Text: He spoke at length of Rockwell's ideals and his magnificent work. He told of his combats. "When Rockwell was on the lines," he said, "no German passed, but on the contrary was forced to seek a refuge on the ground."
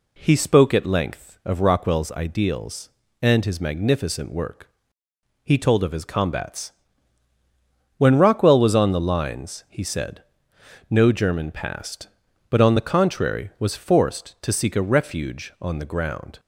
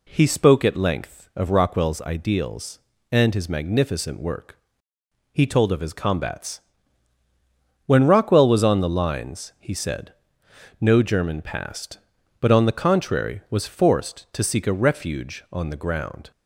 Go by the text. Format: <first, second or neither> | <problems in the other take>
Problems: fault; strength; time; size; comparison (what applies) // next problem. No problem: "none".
neither | none